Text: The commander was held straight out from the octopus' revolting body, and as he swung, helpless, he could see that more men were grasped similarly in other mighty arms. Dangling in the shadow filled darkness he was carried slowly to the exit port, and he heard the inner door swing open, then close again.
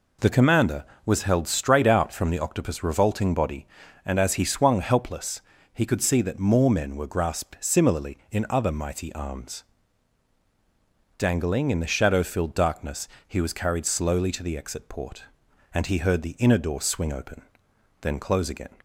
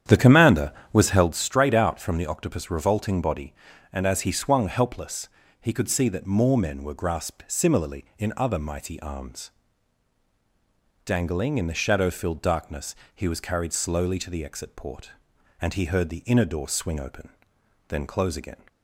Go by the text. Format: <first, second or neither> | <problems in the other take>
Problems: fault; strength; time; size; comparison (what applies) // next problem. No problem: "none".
first | starts louder than the rest; strong; until 1.3 s; 9.5 dB // pauses between "darkness" and "he"; slight; at 12.9 s; 0.20 s long; slight in the first